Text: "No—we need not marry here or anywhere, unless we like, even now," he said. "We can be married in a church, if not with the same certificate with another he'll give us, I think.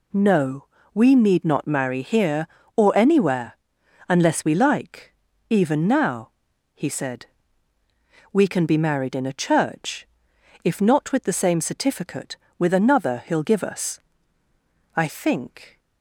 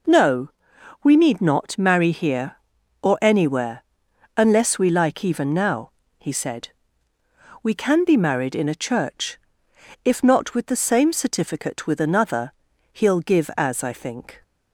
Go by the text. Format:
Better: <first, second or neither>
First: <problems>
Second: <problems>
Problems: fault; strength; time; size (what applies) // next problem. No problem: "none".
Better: first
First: none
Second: pauses between "another" and "he'll"; at 12.5 s; 0.40 s long // says "as" for "us"; at 13.5 s